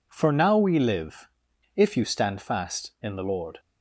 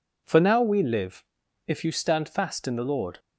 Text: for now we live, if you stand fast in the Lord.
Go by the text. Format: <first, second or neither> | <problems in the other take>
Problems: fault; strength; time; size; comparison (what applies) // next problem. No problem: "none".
neither | none